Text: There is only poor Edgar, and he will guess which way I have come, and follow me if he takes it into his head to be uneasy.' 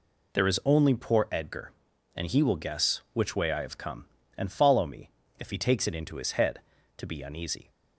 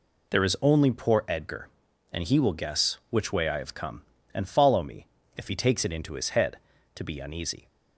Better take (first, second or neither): neither